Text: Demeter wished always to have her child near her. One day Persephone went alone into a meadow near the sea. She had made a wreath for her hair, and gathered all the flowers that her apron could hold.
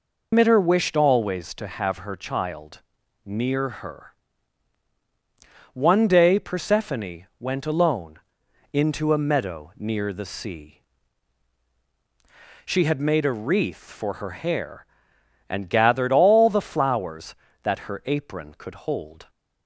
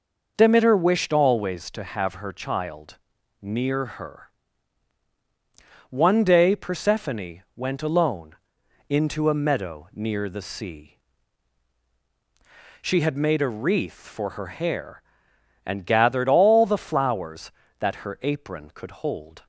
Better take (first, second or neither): second